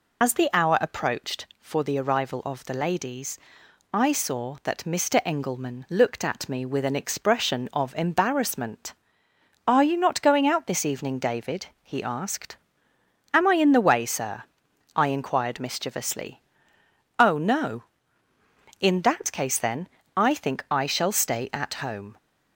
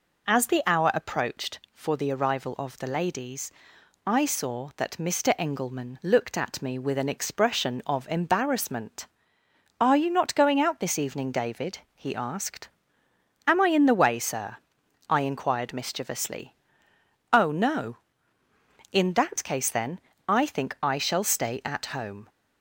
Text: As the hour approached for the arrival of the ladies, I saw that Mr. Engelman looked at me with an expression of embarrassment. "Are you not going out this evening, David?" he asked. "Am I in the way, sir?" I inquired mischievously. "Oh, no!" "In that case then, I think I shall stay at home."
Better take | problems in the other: second | loses the start of "As"; at 0.2 s; 75 ms

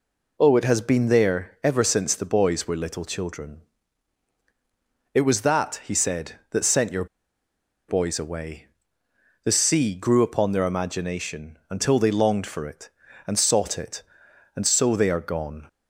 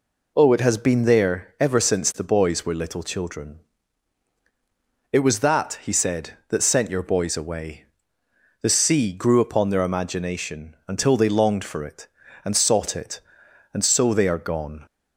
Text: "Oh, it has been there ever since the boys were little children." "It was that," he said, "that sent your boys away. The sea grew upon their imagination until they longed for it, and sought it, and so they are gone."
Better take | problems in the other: second | pauses between "your" and "boys"; noticeable; at 7.0 s; 0.83 s long

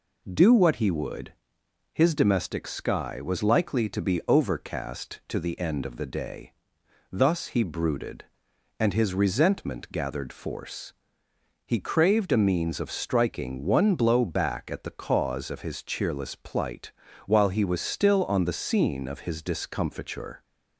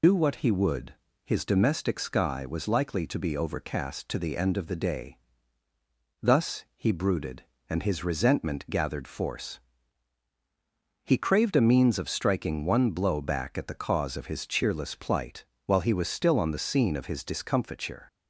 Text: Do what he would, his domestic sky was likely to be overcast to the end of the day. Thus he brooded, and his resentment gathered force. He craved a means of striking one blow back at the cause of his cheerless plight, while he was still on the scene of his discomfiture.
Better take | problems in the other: first | loses the start of "Do"; at 0.0 s; 105 ms

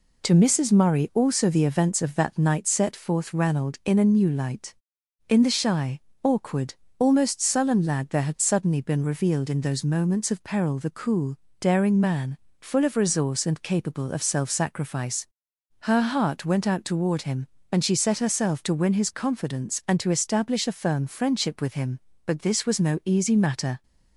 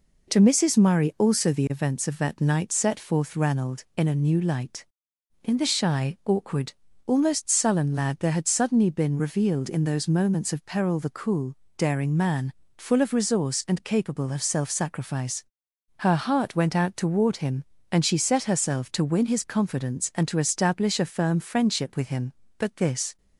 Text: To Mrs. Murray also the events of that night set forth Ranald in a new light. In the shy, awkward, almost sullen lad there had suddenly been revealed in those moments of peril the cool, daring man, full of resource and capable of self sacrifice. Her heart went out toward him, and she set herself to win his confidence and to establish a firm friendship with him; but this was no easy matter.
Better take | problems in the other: first | stops before "was no easy matter"; at 23.1 s

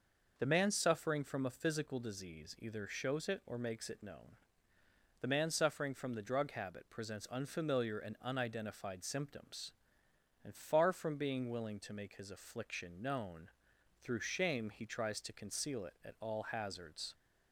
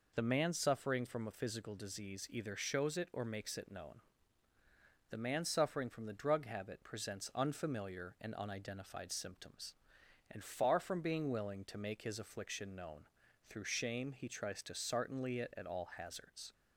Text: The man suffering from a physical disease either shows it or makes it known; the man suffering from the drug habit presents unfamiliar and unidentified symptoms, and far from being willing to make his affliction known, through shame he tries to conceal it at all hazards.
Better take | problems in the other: first | says "sartenly" for "conceal"; at 14.7 s

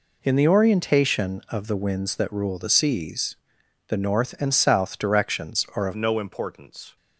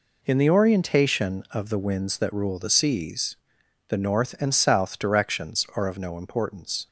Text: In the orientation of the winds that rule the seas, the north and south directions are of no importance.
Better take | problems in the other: second | changes voice at "no"; from 5.9 s on; 1.0 s long

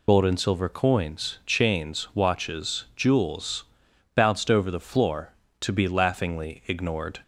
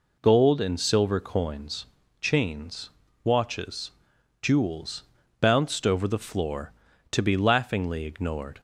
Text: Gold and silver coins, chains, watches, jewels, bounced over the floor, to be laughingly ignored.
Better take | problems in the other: second | loses the start of "Gold"; at 0.0 s; 60 ms

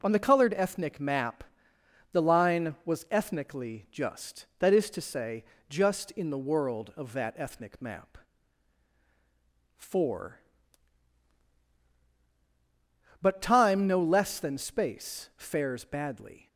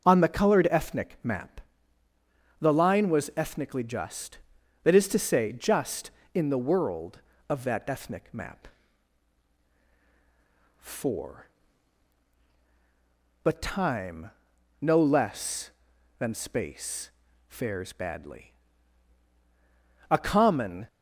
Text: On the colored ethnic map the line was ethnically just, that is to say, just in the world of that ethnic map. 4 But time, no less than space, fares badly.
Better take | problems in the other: first | starts louder than the rest; until 1.0 s; 6.5 dB // pauses between "map" and "the"; noticeable; at 1.6 s; 0.98 s long; noticeable in the first // goes on to say "A common"; noticeable; from 20.0 s on; 0.78 s long

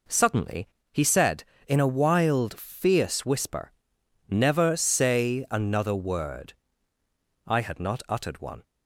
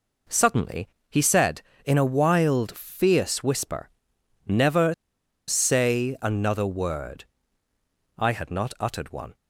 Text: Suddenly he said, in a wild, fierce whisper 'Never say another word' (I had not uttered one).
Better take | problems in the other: first | pauses between "Suddenly" and "he"; slight; at 0.8 s; 0.22 s long; slight in the first // pauses between "whisper" and "Never"; noticeable; at 3.8 s; 0.60 s long; noticeable in the first // pauses between "Never" and "say"; noticeable; at 4.9 s; 0.54 s long

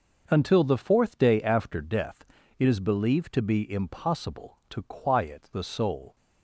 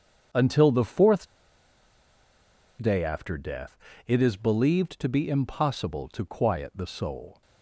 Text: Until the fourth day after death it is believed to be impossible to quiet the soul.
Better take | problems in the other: first | starts louder than the rest; strong; until 2.8 s; 7.5 dB; noticeable in the first // pauses between "fourth" and "day"; strong; at 1.2 s; 1.5 s long // pauses between "death" and "it"; slight; at 3.7 s; 0.32 s long; slight in the first

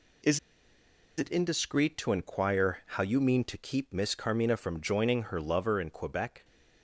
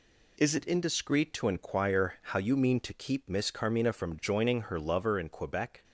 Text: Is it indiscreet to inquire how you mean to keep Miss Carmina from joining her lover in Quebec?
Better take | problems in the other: second | pauses between "Is" and "it"; noticeable; at 0.3 s; 0.79 s long

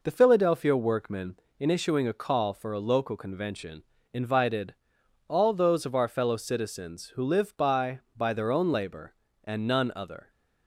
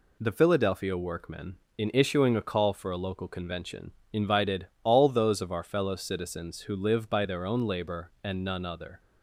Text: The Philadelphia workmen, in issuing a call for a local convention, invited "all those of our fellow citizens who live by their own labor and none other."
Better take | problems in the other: second | pauses between "invited" and "all"; noticeable; at 4.7 s; 0.54 s long; slight in the second // says "by" twice; at 8.1 s

